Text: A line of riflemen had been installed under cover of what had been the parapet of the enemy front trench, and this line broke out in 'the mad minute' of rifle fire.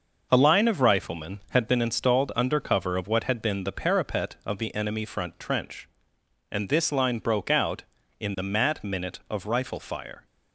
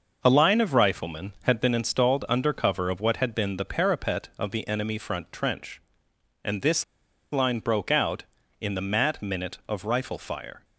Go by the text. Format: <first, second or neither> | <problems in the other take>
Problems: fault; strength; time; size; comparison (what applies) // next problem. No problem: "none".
first | pauses between "this" and "line"; noticeable; at 6.8 s; 0.47 s long